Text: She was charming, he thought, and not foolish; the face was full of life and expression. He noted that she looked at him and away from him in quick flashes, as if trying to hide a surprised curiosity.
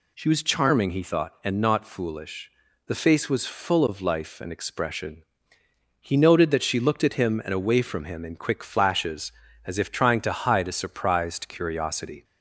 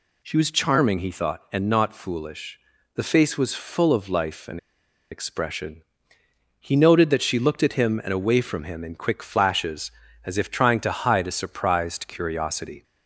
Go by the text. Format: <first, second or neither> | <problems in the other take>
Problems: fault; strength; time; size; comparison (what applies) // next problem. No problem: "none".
first | pauses between "and" and "expression"; noticeable; at 4.5 s; 0.54 s long